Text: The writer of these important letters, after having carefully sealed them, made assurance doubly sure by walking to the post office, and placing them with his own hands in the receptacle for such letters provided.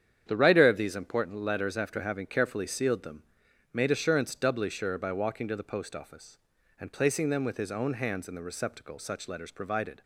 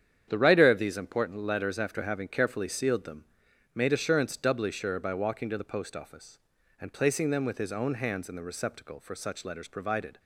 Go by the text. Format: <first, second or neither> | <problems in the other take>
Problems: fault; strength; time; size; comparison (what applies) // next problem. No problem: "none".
second | starts louder than the rest; strong; until 1.2 s; 8.5 dB; strong in the second // skips "for"; at 8.9 s